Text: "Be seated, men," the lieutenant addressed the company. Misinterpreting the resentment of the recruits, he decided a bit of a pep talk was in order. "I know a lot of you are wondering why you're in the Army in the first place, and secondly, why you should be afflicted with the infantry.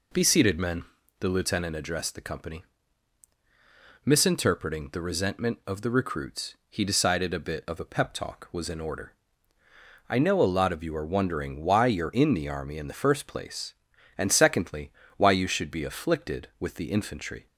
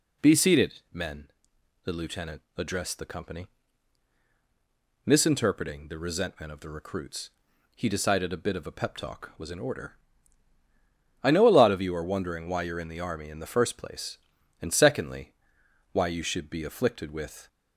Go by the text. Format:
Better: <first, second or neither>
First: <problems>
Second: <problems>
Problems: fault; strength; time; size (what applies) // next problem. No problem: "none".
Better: first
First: none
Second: stops before "the infantry"; at 17.4 s